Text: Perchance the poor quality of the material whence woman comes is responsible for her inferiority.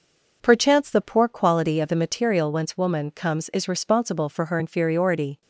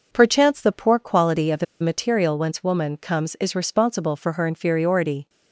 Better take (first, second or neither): first